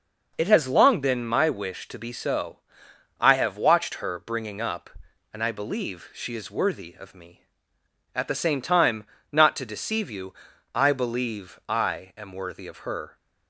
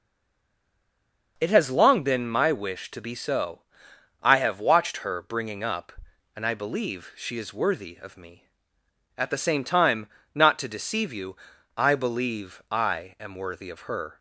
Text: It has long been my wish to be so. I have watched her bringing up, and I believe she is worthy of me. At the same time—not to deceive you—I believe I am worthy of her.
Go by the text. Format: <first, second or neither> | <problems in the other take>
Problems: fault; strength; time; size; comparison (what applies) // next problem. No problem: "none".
first | stays silent before the first word; noticeable; until 1.3 s; 1.3 s long